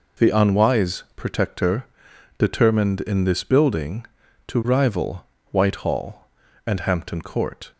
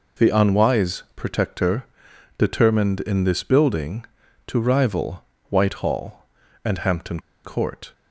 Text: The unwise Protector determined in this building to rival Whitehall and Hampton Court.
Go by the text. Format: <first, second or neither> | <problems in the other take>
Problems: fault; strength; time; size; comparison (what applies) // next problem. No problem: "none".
first | pauses between "Protector" and "determined"; noticeable; at 1.8 s; 0.54 s long; noticeable in the first // pauses between "rival" and "Whitehall"; slight; at 5.2 s; 0.26 s long; slight in the first // pauses between "Hampton" and "Court"; slight; at 7.1 s; 0.24 s long